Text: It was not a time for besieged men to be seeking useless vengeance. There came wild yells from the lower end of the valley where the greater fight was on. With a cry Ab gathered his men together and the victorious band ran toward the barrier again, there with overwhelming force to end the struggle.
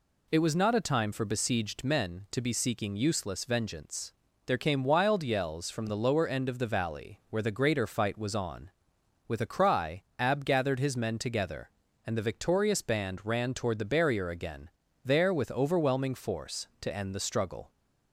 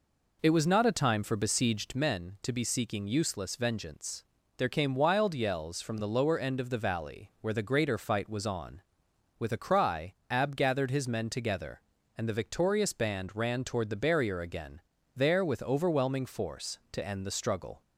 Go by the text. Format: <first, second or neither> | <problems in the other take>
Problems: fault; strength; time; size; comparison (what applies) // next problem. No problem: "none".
first | starts louder than the rest; noticeable; until 2.0 s; 4.5 dB // pauses between "cry" and "Ab"; slight; at 10.1 s; 0.16 s long; slight in the first